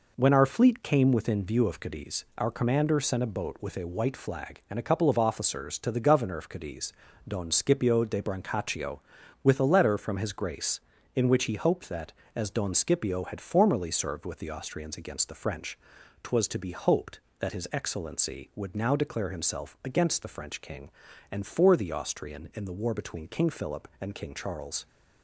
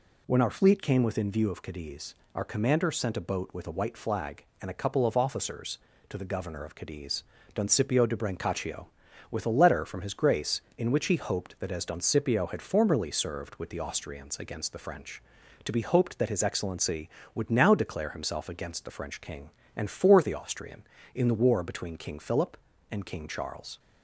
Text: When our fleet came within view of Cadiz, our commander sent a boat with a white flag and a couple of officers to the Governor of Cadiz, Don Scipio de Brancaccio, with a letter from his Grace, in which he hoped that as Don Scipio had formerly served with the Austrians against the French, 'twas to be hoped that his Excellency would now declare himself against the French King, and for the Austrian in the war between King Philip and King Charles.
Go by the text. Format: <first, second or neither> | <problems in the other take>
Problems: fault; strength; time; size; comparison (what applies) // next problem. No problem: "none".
first | skips "twas"; at 15.4 s